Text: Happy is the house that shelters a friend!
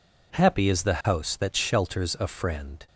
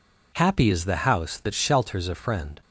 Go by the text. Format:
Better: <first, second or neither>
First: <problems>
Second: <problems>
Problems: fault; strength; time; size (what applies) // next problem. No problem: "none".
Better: neither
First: none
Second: none